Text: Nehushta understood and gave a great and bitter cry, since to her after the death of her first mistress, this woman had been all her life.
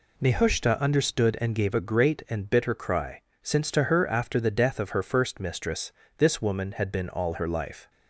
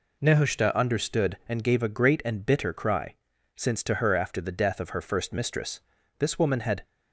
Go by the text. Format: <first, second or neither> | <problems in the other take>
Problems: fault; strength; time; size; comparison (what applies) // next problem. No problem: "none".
first | stops before "been all her life"; at 6.8 s